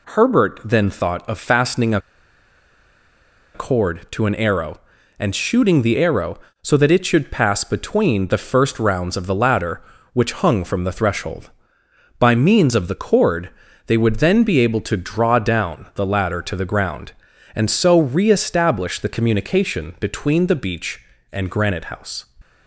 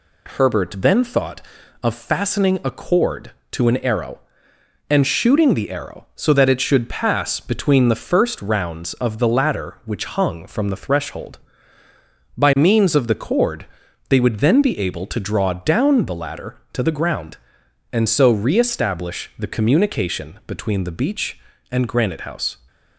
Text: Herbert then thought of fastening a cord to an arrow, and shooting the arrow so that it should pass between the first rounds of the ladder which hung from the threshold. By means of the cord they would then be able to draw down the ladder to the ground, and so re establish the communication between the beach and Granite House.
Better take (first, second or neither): second